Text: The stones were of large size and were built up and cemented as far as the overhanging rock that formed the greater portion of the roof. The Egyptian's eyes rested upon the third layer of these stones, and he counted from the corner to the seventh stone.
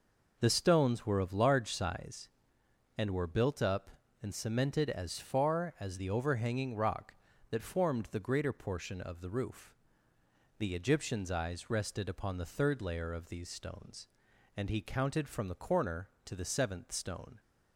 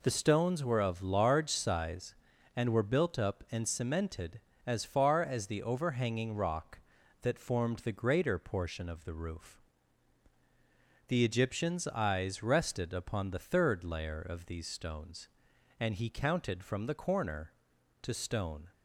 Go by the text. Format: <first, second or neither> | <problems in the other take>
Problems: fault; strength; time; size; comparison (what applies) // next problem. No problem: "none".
first | skips "the seventh"; at 18.1 s